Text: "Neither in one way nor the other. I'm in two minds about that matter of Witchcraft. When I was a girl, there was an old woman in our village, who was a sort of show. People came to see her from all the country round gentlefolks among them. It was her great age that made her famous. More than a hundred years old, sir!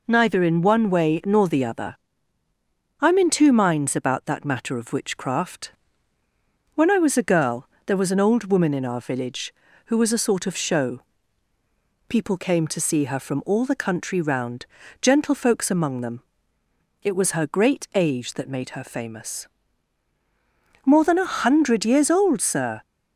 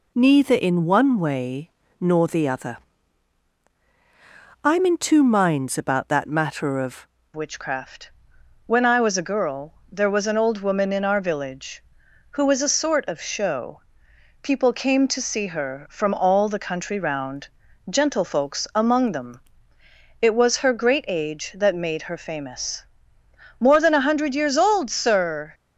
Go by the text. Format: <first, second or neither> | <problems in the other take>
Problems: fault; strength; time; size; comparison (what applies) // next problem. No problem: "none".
first | pauses between "way" and "nor"; slight; at 1.7 s; 0.30 s long // changes voice at "Witchcraft"; from 7.3 s on; 18.2 s long // pauses between "round" and "gentlefolks"; at 17.4 s; 0.42 s long; slight in the first